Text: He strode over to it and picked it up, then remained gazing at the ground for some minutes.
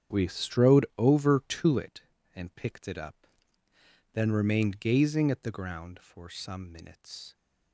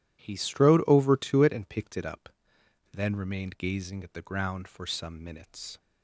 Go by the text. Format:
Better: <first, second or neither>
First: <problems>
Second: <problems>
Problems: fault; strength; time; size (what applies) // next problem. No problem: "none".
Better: second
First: starts louder than the rest; strong; until 1.2 s; 9 dB // says "We" for "He"; at 0.1 s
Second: none